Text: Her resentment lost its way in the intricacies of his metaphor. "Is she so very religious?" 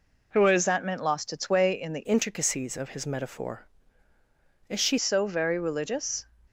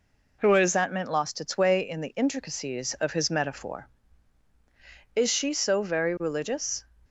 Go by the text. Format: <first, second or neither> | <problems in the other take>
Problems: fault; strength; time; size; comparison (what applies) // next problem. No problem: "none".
second | changes voice from "intricacies" to "she"; from 2.0 to 4.9 s; 2.9 s long